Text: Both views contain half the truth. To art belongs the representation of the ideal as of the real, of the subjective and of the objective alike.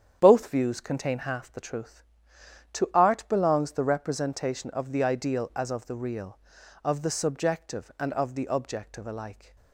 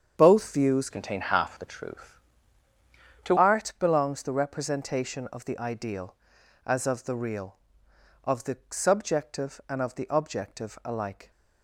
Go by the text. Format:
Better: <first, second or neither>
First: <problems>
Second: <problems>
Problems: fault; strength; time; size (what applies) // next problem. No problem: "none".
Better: first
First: starts louder than the rest; strong; until 1.2 s; 8.5 dB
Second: starts louder than the rest; strong; until 1.1 s; 7.5 dB // changes voice from "contain" to "To"; from 0.8 to 3.3 s; 2.5 s long